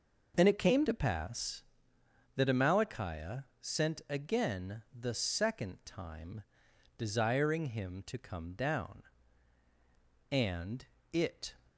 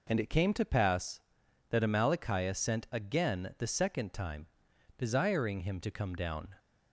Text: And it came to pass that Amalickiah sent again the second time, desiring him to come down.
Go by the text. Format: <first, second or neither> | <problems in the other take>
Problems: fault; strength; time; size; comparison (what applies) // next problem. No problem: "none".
second | pauses between "Amalickiah" and "sent"; slight; at 3.4 s; 0.18 s long // pauses between "again" and "the"; slight; at 4.8 s; 0.16 s long // goes on to say "And it"; noticeable; from 10.2 s on; 1.2 s long